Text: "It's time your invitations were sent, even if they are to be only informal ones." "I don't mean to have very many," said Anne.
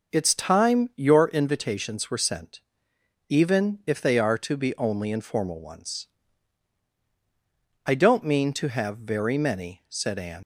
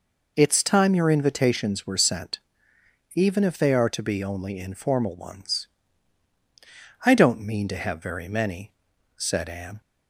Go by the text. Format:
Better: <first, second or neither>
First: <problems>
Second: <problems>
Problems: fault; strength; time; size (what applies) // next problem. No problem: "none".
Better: second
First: starts louder than the rest; until 1.2 s; 6 dB // leaves "Anne" unfinished; at 10.4 s; 95 ms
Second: none